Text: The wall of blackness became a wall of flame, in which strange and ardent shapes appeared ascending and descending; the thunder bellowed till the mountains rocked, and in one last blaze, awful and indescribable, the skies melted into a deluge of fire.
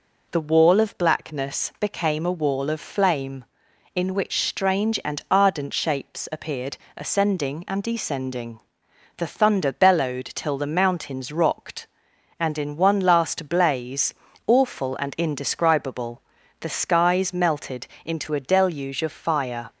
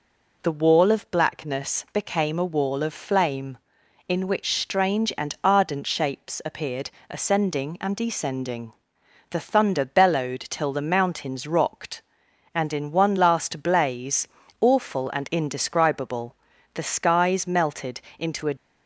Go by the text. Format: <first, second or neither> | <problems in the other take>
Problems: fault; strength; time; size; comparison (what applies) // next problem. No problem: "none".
first | pauses between "appeared" and "ascending"; slight; at 6.8 s; 0.20 s long; slight in the first // pauses between "melted" and "into"; slight; at 18.0 s; 0.16 s long; slight in the first // stops before "deluge of fire"; at 18.5 s